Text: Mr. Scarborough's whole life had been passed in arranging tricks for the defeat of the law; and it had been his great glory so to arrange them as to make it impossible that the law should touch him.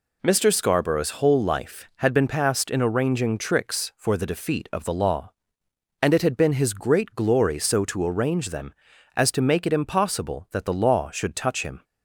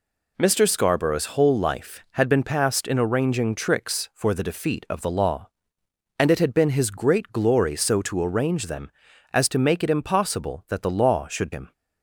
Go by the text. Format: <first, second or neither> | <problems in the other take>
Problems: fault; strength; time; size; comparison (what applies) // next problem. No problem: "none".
first | skips "touch"; at 11.5 s